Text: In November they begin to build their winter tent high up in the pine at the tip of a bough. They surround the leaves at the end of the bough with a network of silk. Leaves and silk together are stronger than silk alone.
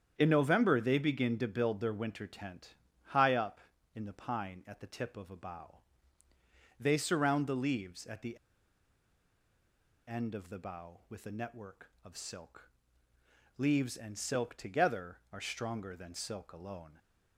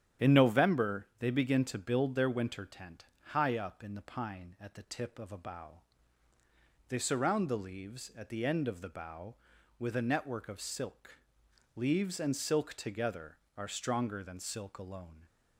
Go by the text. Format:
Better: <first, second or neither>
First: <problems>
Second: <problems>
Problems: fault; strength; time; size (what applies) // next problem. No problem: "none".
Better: second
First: starts louder than the rest; strong; until 1.1 s; 8.5 dB // pauses between "tent" and "high"; slight; at 2.7 s; 0.30 s long // pauses between "the" and "end"; strong; at 8.3 s; 1.7 s long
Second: starts louder than the rest; strong; until 1.3 s; 9 dB // pauses between "tent" and "high"; slight; at 3.0 s; 0.22 s long